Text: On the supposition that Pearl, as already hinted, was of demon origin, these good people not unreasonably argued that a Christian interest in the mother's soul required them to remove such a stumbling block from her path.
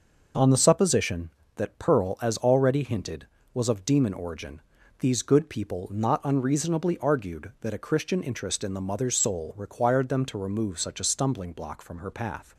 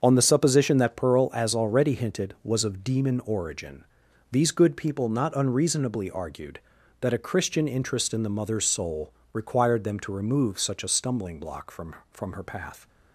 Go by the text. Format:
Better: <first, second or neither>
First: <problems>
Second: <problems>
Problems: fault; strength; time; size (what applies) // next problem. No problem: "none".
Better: first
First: none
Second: starts louder than the rest; until 1.0 s; 6.5 dB // pauses between "soul" and "required"; slight; at 9.1 s; 0.18 s long // says "from" twice; at 12.1 s